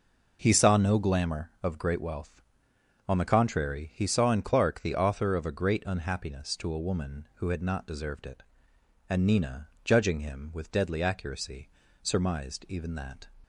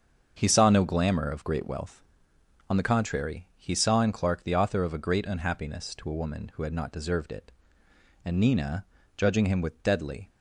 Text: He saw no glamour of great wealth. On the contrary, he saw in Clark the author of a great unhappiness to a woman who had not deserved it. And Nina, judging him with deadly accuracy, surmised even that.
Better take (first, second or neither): first